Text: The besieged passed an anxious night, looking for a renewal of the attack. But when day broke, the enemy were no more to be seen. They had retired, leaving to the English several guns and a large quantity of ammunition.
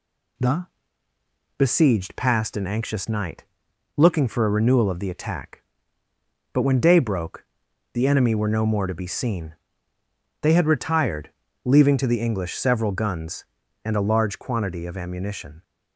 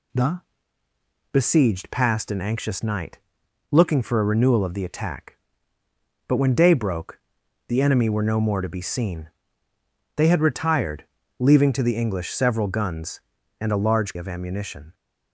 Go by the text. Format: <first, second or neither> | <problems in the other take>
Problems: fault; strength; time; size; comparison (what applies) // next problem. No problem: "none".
first | pauses between "The" and "besieged"; noticeable; at 0.4 s; 0.90 s long; noticeable in the first // skips "quantity"; at 14.1 s